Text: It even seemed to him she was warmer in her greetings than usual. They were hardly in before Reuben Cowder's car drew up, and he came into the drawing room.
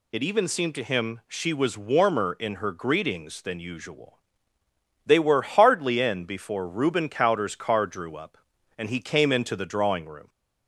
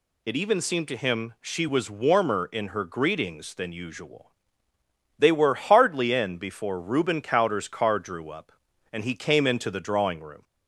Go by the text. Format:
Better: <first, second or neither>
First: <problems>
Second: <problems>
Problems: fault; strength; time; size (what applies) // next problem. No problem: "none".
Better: neither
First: none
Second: none